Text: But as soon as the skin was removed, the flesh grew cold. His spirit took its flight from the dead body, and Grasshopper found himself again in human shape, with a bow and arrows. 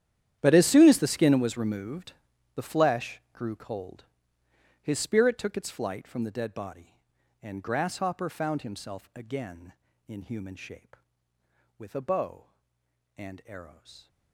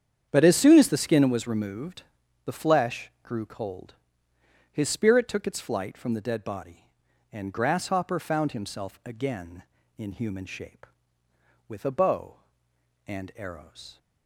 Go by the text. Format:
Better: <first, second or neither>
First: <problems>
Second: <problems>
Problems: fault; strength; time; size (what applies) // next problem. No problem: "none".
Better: second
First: gets quieter; strong; throughout; 18.5 dB // starts louder than the rest; strong; until 1.4 s; 10.5 dB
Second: starts louder than the rest; strong; until 1.3 s; 8.5 dB